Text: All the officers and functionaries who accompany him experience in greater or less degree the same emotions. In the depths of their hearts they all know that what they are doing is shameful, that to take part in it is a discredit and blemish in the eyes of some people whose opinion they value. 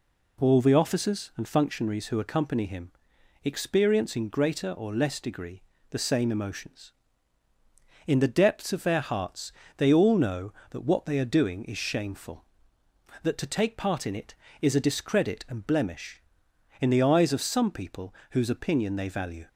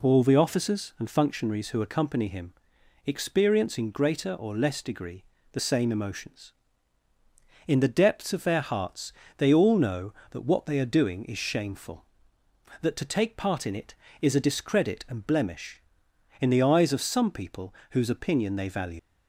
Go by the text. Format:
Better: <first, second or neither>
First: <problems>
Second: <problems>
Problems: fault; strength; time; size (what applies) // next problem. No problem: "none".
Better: first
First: pauses between "him" and "experience"; noticeable; at 2.9 s; 0.52 s long // pauses between "degree" and "the"; slight; at 5.6 s; 0.28 s long // pauses between "hearts" and "they"; slight; at 9.5 s; 0.26 s long // pauses between "people" and "whose"; slight; at 18.1 s; 0.16 s long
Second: pauses between "him" and "experience"; noticeable; at 2.5 s; 0.52 s long // pauses between "degree" and "the"; slight; at 5.2 s; 0.28 s long // pauses between "hearts" and "they"; slight; at 9.1 s; 0.26 s long // pauses between "people" and "whose"; slight; at 17.7 s; 0.16 s long // leaves "value" unfinished; at 18.9 s; 85 ms